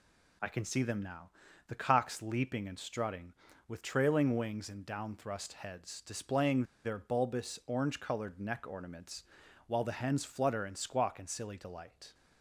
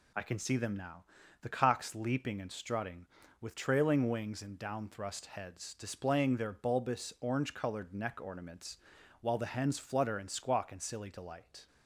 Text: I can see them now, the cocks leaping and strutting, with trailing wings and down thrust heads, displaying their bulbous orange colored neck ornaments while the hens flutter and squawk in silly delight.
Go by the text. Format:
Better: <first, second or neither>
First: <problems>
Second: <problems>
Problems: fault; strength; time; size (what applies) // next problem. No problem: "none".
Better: second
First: pauses between "displaying" and "their"; slight; at 6.6 s; 0.21 s long // pauses between "ornaments" and "while"; at 9.2 s; 0.44 s long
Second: pauses between "ornaments" and "while"; at 8.7 s; 0.44 s long